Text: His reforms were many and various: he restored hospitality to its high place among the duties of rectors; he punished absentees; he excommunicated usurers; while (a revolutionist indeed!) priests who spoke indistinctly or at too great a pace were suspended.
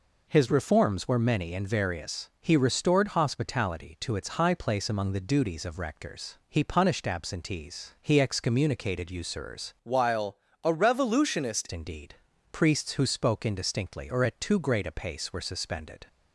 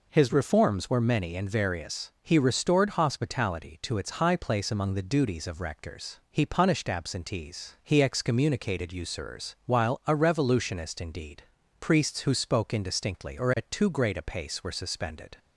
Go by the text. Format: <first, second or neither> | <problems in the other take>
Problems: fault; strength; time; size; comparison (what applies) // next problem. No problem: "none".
second | changes voice from "while" to "revolutionist"; from 9.8 to 11.6 s; 1.8 s long